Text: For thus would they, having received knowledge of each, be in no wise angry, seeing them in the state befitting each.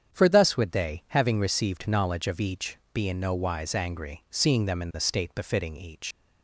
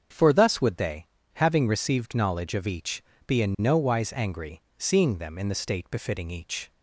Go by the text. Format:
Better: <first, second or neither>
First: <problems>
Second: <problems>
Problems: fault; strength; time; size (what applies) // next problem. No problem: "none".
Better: second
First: starts louder than the rest; strong; until 1.1 s; 8 dB // leaves "each" unfinished; at 6.1 s; 95 ms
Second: starts louder than the rest; strong; until 1.4 s; 7.5 dB